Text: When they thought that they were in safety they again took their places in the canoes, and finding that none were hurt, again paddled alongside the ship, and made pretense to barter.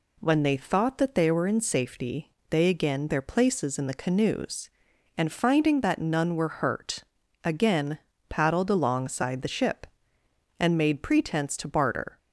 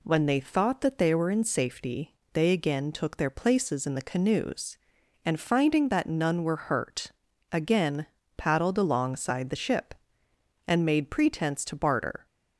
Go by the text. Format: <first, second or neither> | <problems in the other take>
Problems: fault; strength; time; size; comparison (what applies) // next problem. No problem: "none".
second | pauses between "safety" and "they"; slight; at 2.3 s; 0.20 s long; slight in the second // skips "took"; at 3.0 s // pauses between "again" and "paddled"; slight; at 7.9 s; 0.28 s long; slight in the second